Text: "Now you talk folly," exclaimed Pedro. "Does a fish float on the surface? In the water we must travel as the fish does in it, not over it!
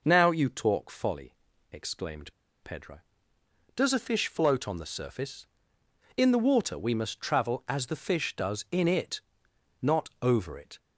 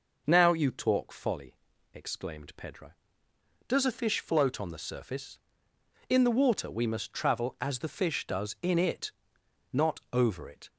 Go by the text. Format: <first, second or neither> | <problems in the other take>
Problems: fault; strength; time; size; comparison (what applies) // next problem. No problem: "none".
second | pauses between "exclaimed" and "Pedro"; slight; at 2.3 s; 0.30 s long